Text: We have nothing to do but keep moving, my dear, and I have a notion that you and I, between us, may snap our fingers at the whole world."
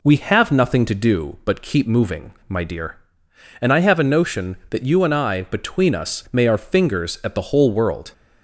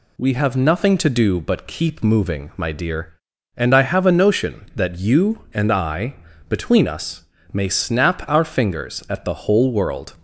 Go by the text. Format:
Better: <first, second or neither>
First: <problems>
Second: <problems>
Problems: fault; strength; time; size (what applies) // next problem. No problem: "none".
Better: second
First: skips "snap"; at 6.4 s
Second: none